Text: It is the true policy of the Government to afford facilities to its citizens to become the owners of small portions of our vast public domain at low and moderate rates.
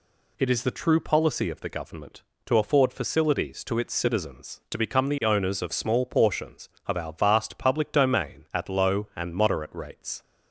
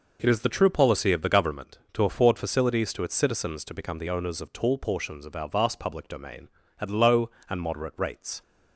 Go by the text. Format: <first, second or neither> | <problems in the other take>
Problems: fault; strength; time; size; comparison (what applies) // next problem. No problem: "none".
first | says "tall" for "small"; at 4.5 s